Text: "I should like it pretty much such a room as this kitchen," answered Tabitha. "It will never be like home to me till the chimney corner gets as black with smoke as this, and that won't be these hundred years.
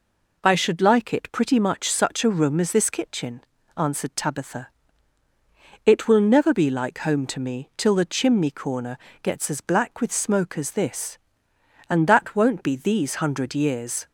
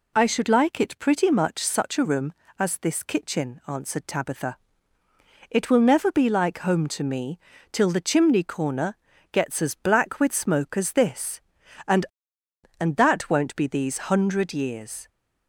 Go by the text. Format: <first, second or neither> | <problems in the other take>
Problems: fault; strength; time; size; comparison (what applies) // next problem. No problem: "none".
first | pauses between "me" and "till"; slight; at 7.3 s; 0.34 s long // pauses between "corner" and "gets"; slight; at 8.9 s; 0.36 s long; slight in the first // says "and" twice; at 12.7 s